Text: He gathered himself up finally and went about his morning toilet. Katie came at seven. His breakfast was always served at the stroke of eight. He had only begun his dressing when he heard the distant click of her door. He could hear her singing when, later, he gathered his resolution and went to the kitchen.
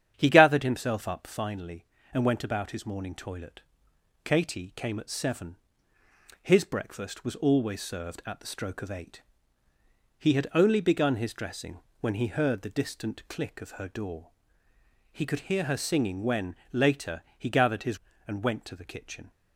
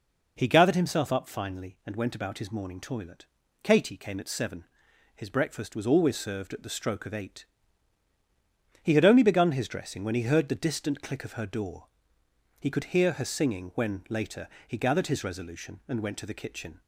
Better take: second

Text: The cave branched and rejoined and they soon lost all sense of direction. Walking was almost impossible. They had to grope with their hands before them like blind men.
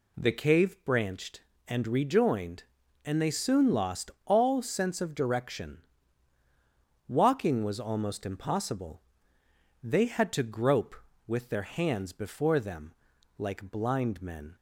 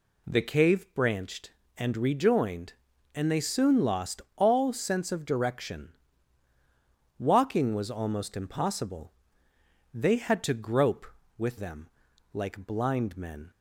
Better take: first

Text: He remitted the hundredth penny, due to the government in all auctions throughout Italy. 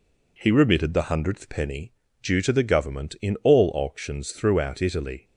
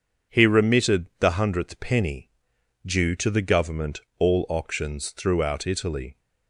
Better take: first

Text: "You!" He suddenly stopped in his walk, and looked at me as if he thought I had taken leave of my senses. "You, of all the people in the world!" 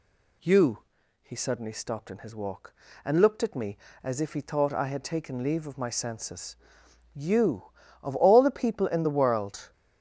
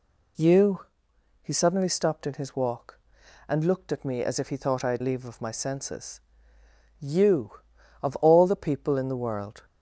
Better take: first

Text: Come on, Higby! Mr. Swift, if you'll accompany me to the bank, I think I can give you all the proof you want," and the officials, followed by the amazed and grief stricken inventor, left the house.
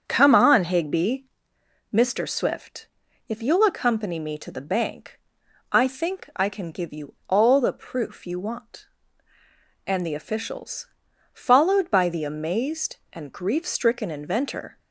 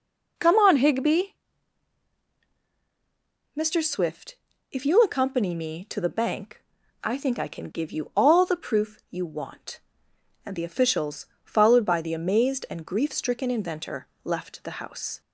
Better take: second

